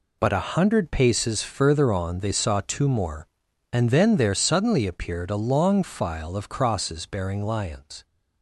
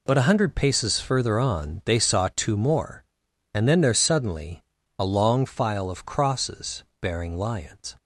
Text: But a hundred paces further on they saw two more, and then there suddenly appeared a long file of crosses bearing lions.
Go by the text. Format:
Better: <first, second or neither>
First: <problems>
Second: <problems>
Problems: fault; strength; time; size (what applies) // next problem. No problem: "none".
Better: first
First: none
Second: skips "appeared"; at 4.8 s // pauses between "crosses" and "bearing"; slight; at 6.8 s; 0.16 s long